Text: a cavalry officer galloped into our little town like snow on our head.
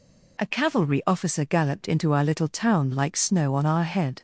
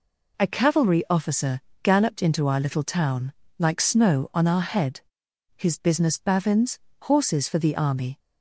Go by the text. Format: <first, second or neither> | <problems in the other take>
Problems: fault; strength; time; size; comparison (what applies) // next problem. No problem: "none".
first | pauses between "officer" and "galloped"; slight; at 1.6 s; 0.24 s long // pauses between "town" and "like"; slight; at 3.3 s; 0.26 s long // goes on to say "His business bavins horses for the army"; strong; from 5.5 s on; 2.6 s long